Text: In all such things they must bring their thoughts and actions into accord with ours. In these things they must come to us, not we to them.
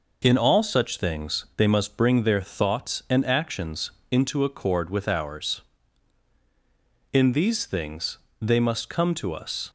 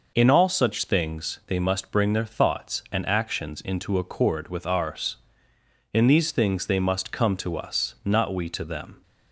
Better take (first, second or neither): second